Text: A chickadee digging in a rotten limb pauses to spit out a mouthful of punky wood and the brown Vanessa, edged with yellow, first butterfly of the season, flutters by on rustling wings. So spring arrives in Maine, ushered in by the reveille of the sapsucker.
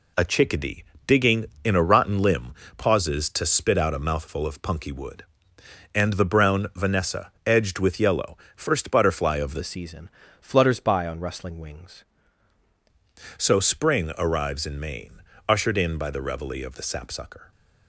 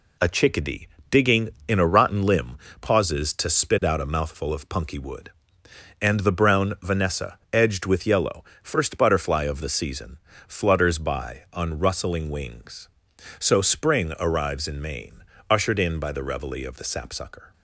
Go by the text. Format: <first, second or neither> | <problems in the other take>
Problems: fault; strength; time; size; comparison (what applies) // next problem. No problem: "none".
second | pauses between "chickadee" and "digging"; slight; at 0.8 s; 0.24 s long; slight in the second // pauses between "limb" and "pauses"; slight; at 2.5 s; 0.24 s long; slight in the second // changes voice from "season" to "wings"; from 9.6 to 12.0 s; 2.4 s long